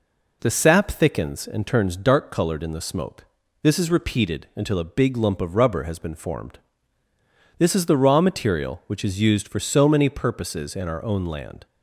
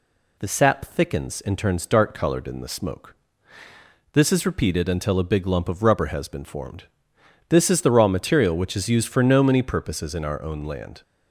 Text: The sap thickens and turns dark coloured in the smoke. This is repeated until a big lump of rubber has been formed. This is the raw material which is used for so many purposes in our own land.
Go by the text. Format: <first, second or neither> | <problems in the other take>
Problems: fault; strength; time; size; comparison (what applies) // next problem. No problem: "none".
first | says "no" for "so"; at 9.2 s